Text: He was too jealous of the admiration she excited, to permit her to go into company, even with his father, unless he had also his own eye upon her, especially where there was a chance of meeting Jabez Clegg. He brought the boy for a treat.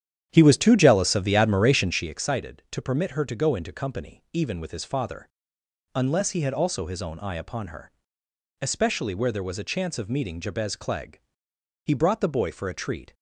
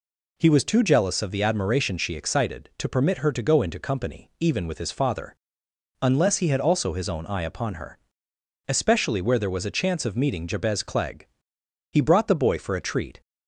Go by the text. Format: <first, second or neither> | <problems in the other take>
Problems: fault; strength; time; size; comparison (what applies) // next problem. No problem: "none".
second | starts louder than the rest; strong; until 2.2 s; 9.5 dB